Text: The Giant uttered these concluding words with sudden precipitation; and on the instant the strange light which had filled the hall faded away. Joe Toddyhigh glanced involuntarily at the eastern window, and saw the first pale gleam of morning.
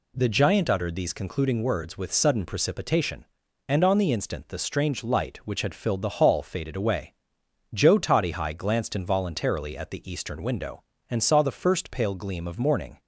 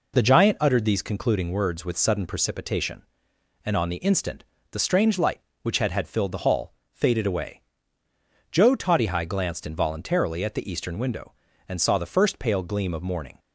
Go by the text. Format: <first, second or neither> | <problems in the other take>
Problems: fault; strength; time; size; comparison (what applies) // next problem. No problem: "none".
first | pauses between "instant" and "the"; slight; at 4.4 s; 0.26 s long // says "had" twice; at 5.9 s // pauses between "hall" and "faded"; slight; at 6.7 s; 0.20 s long